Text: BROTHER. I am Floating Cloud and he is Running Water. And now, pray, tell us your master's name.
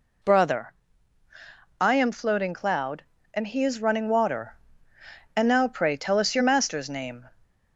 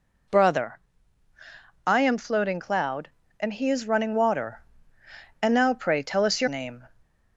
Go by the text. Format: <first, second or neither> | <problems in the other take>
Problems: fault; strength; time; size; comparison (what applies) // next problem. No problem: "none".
first | skips "master's"; at 6.4 s